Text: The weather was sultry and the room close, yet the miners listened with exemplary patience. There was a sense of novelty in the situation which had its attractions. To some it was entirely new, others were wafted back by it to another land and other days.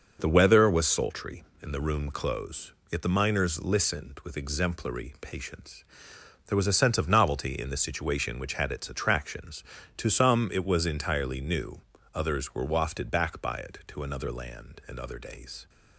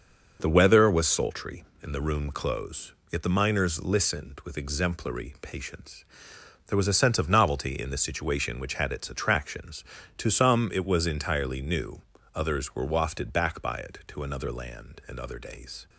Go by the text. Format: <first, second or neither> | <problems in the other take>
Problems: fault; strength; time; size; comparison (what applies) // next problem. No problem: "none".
neither | none